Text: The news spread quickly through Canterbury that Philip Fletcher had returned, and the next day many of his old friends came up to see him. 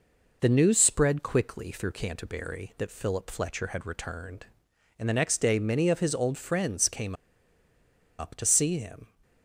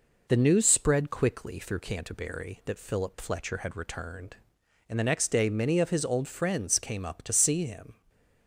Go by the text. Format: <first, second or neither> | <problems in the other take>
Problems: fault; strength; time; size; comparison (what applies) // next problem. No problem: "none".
second | pauses between "came" and "up"; at 7.1 s; 1.0 s long